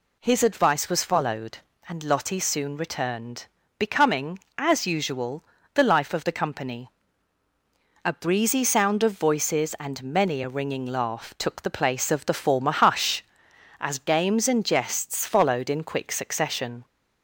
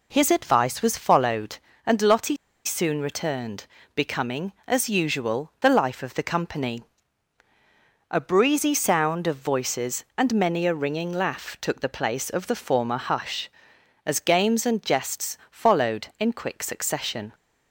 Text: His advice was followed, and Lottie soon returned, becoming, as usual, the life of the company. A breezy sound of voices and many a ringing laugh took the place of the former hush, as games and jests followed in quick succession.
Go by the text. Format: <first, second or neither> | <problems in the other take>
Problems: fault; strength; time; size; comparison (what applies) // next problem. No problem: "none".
first | pauses between "Lottie" and "soon"; slight; at 2.3 s; 0.30 s long